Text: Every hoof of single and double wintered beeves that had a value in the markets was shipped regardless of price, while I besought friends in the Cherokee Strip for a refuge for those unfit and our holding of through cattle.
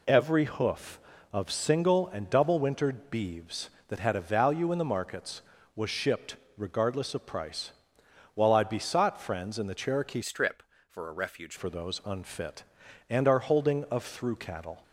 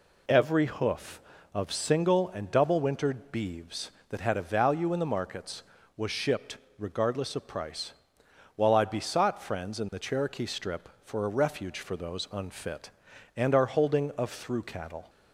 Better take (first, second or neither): second